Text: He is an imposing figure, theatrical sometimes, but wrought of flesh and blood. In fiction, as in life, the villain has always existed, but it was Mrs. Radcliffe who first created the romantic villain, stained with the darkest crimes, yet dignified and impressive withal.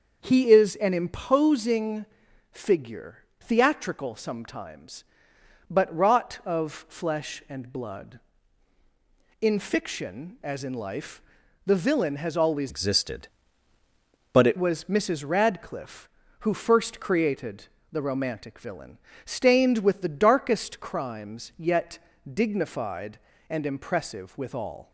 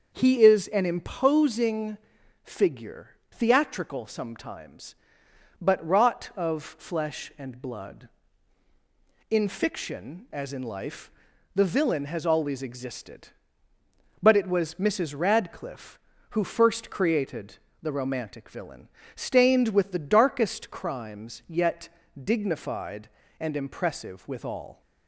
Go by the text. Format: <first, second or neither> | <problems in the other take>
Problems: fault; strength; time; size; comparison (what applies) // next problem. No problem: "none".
second | starts louder than the rest; until 1.2 s; 6 dB; also in the second // pauses between "imposing" and "figure"; noticeable; at 2.0 s; 0.46 s long; noticeable in the second // changes voice from "existed" to "it"; from 12.6 to 14.5 s; 1.9 s long // pauses between "created" and "the"; slight; at 17.6 s; 0.24 s long; slight in the second // pauses between "yet" and "dignified"; slight; at 21.9 s; 0.32 s long; slight in the second